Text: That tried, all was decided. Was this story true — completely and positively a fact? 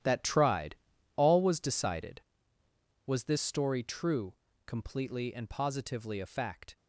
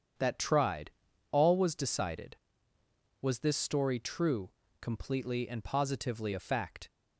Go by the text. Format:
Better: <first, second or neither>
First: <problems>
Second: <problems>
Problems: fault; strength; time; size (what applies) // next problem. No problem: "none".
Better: second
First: gets quieter; strong; throughout; 14 dB // starts louder than the rest; strong; until 1.4 s; 11.5 dB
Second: starts louder than the rest; strong; until 1.6 s; 8 dB